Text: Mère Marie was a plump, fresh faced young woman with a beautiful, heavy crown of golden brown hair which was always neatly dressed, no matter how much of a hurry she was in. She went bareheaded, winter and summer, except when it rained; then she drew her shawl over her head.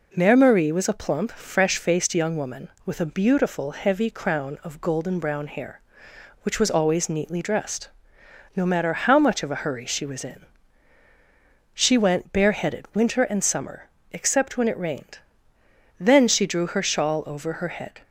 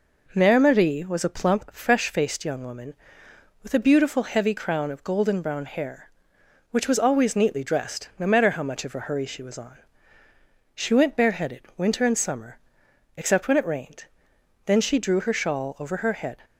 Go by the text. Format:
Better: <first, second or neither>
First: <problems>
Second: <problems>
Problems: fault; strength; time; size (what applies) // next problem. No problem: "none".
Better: first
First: none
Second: says "on" for "in"; at 9.5 s